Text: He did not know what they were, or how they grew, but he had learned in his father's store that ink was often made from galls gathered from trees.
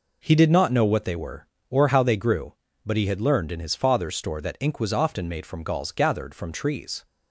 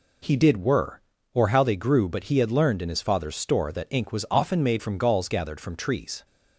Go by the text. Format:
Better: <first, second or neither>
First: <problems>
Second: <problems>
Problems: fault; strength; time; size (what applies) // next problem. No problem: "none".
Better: first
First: none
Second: skips "not know what they"; at 0.6 s